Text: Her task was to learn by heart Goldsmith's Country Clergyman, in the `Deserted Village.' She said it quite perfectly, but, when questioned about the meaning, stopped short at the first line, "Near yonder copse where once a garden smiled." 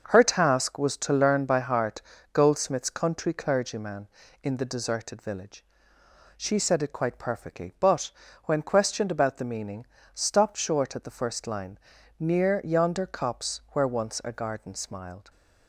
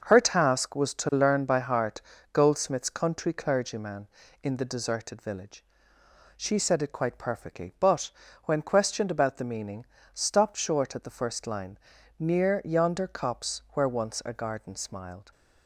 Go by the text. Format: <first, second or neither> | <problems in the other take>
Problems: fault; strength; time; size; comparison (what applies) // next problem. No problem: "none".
neither | starts louder than the rest; the same in both // pauses between "heart" and "Goldsmith's"; slight; the same in both